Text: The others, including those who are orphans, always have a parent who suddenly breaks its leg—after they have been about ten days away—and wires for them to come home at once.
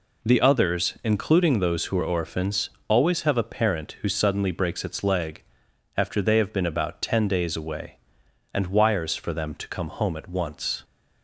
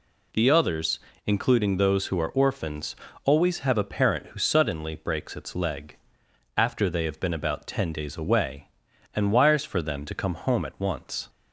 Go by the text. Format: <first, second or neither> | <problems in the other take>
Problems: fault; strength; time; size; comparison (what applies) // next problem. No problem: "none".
neither | none